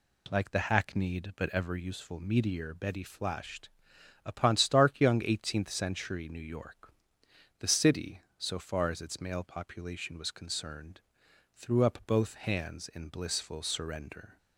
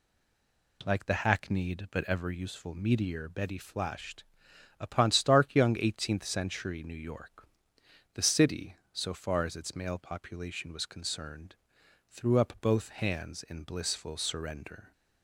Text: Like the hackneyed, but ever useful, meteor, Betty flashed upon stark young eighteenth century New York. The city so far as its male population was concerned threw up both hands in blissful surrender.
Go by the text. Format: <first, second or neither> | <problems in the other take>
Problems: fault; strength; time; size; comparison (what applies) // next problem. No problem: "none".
first | stays silent before the first word; slight; until 0.8 s; 0.8 s long // pauses between "flashed" and "upon"; noticeable; at 4.2 s; 0.56 s long; noticeable in the first // pauses between "concerned" and "threw"; noticeable; at 11.5 s; 0.54 s long; noticeable in the first